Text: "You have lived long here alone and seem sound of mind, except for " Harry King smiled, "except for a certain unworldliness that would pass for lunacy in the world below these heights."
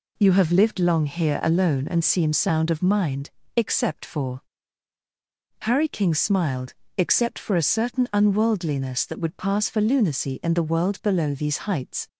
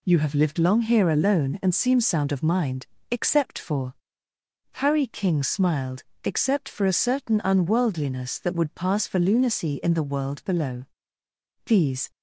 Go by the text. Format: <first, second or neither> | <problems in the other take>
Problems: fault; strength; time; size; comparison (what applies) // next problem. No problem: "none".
first | pauses between "below" and "these"; noticeable; at 10.8 s; 0.82 s long // stops before "heights"; at 12.1 s